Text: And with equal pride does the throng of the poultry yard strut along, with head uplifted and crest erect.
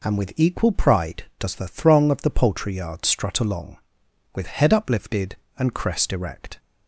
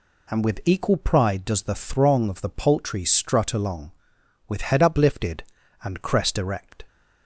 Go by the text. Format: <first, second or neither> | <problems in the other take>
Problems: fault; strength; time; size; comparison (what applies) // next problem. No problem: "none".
first | skips "yard"; at 3.0 s